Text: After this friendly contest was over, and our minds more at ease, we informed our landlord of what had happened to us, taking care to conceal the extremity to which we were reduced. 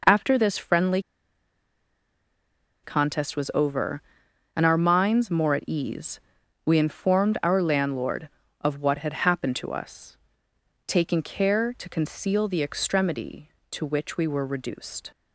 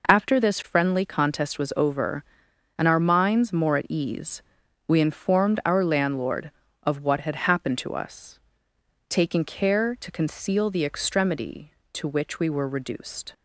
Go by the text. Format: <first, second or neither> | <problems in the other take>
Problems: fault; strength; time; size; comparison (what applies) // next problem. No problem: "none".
second | pauses between "friendly" and "contest"; strong; at 1.0 s; 1.8 s long